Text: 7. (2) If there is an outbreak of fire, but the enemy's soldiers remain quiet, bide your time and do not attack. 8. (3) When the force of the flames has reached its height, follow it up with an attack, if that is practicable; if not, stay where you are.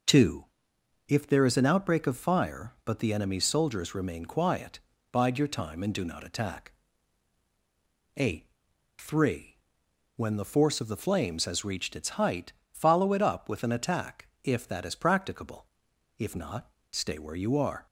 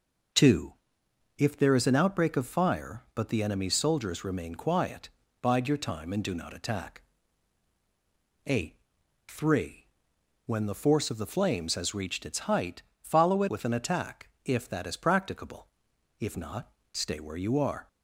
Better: first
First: none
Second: skips "up"; at 13.4 s

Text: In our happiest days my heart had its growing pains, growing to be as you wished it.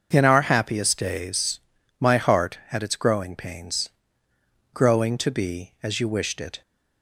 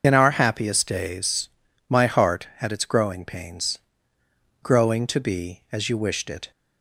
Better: first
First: starts louder than the rest; until 1.1 s; 6.5 dB // pauses between "days" and "my"; at 1.5 s; 0.38 s long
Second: loses the start of "In"; at 0.0 s; 50 ms // starts louder than the rest; until 1.0 s; 6.5 dB // pauses between "days" and "my"; at 1.4 s; 0.38 s long

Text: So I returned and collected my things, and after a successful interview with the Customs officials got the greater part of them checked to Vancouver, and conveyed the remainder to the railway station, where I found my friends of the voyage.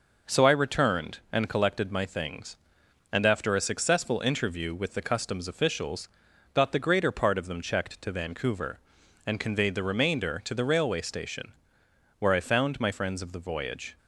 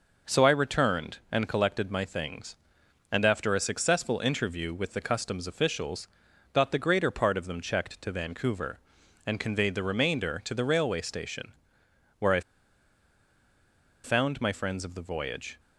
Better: first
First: pauses between "officials" and "got"; noticeable; at 6.0 s; 0.48 s long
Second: pauses between "officials" and "got"; noticeable; at 6.0 s; 0.48 s long // pauses between "I" and "found"; strong; at 12.4 s; 1.6 s long

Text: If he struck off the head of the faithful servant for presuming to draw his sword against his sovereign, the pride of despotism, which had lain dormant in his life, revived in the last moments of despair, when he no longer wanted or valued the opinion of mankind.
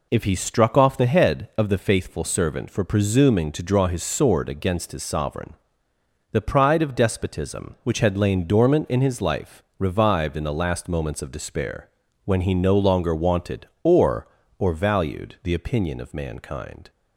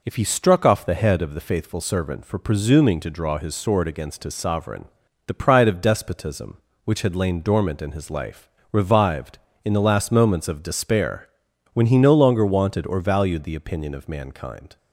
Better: second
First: says "or" twice; at 14.5 s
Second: none

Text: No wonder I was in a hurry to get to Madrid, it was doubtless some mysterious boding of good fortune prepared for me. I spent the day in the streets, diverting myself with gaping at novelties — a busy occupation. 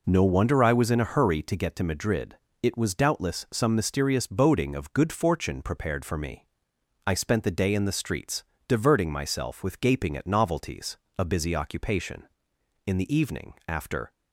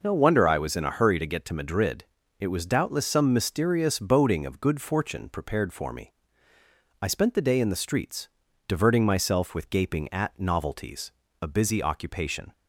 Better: second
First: goes on to say "In the evening after"; noticeable; from 12.8 s on; 1.2 s long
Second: none

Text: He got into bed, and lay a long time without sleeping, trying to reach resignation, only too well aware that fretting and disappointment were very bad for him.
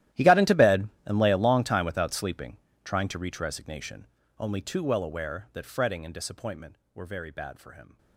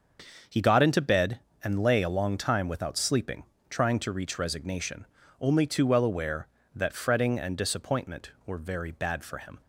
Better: second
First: gets quieter; strong; throughout; 19.5 dB // starts louder than the rest; strong; until 1.3 s; 13.5 dB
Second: starts louder than the rest; until 1.7 s; 6.5 dB

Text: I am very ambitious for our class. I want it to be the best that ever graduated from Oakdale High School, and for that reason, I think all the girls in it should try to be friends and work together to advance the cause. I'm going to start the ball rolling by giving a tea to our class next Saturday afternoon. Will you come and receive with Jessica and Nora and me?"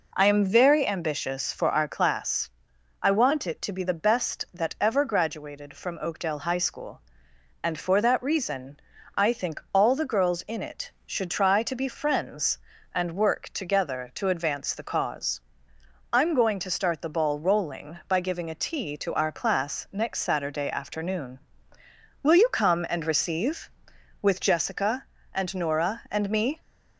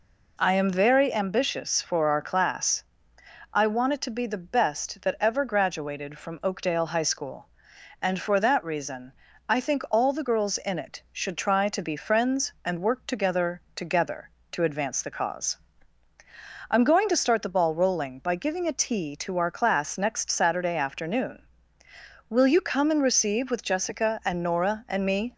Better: first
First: none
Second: says "together" twice; at 13.7 s

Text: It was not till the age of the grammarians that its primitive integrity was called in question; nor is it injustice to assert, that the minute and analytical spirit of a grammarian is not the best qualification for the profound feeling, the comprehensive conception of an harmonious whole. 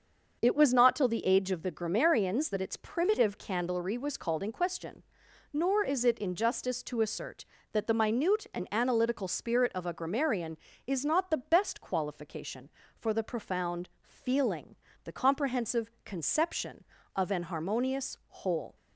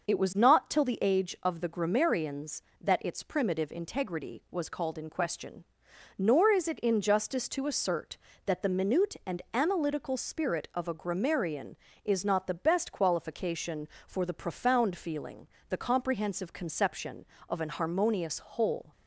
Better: second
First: starts louder than the rest; until 1.4 s; 6.5 dB // says "candlery" for "integrity"; at 3.3 s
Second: starts louder than the rest; noticeable; until 1.1 s; 6 dB

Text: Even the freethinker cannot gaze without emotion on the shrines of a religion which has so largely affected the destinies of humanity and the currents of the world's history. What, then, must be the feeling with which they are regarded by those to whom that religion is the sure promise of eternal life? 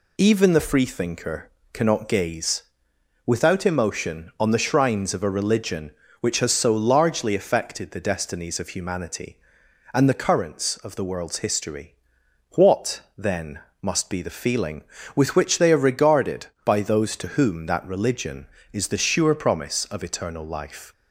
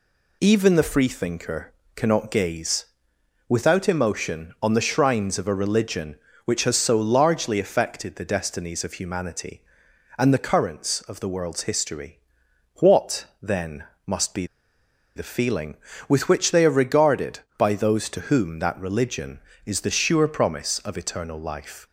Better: first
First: pauses between "freethinker" and "cannot"; slight; at 1.5 s; 0.22 s long // pauses between "gaze" and "without"; noticeable; at 2.6 s; 0.64 s long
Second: pauses between "freethinker" and "cannot"; slight; at 1.7 s; 0.22 s long // pauses between "gaze" and "without"; noticeable; at 2.8 s; 0.64 s long // pauses between "be" and "the"; noticeable; at 14.4 s; 0.70 s long

